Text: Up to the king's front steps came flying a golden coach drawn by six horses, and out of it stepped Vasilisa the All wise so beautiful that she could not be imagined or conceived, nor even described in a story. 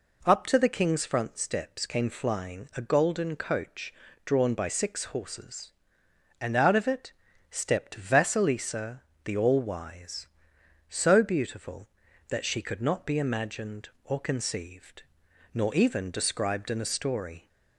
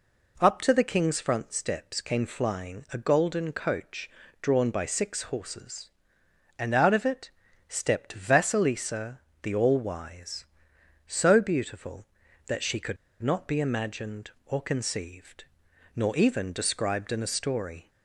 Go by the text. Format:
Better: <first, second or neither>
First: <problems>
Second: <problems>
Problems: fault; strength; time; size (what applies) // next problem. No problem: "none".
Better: first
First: pauses between "coach" and "drawn"; slight; at 3.9 s; 0.32 s long // pauses between "it" and "stepped"; at 7.1 s; 0.38 s long // pauses between "Vasilisa" and "the"; slight; at 9.0 s; 0.20 s long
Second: pauses between "coach" and "drawn"; slight; at 4.1 s; 0.32 s long // pauses between "it" and "stepped"; at 7.3 s; 0.38 s long // pauses between "Vasilisa" and "the"; slight; at 9.2 s; 0.20 s long // pauses between "could" and "not"; slight; at 12.9 s; 0.25 s long